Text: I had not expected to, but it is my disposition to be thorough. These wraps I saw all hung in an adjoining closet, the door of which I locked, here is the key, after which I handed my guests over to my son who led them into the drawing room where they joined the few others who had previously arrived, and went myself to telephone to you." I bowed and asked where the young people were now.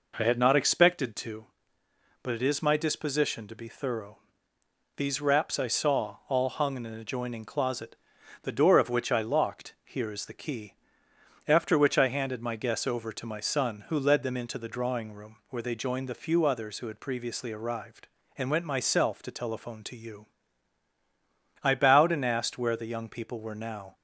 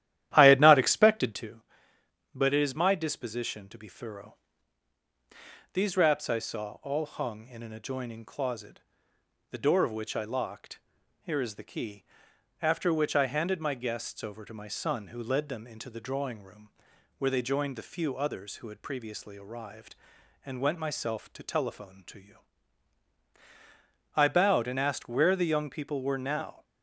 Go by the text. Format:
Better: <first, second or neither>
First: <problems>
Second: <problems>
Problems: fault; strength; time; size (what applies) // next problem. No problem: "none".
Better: first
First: none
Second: starts louder than the rest; strong; until 1.5 s; 12.5 dB // pauses between "room" and "where"; noticeable; at 16.7 s; 0.48 s long